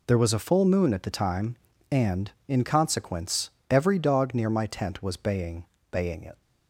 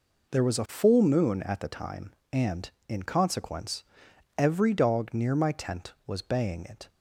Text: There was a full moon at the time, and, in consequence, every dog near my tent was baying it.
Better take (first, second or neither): second